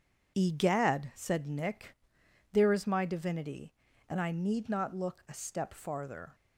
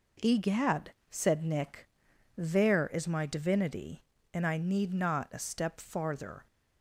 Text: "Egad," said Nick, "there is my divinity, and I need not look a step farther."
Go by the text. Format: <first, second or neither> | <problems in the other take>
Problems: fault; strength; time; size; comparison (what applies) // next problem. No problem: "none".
first | skips "look"; at 5.3 s